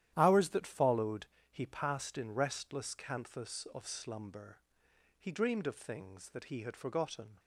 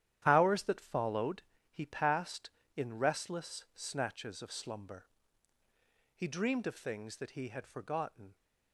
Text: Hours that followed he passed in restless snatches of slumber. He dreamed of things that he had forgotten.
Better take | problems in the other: second | starts louder than the rest; strong; until 1.1 s; 11.5 dB; strong in the second // pauses between "followed" and "he"; slight; at 1.2 s; 0.26 s long; slight in the second // says "canthus" for "snatches"; at 2.9 s

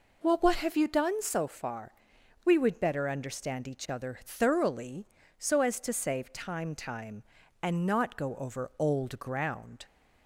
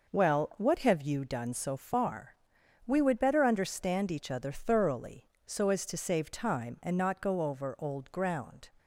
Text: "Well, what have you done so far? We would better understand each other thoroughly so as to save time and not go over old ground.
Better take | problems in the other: second | says "time" twice; at 6.7 s

